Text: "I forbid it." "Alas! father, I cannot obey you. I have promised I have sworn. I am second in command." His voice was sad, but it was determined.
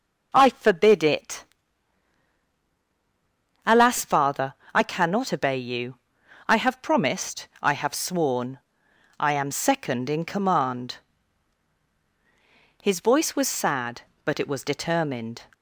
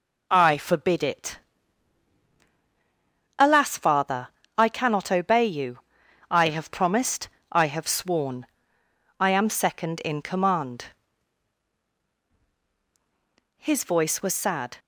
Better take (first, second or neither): first